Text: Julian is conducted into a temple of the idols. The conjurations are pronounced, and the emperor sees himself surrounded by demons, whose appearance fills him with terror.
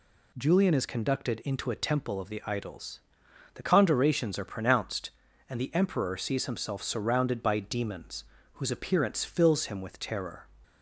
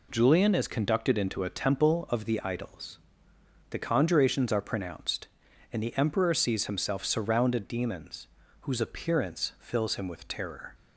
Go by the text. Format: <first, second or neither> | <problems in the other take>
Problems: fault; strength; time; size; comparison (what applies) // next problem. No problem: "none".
first | skips "by"; at 7.6 s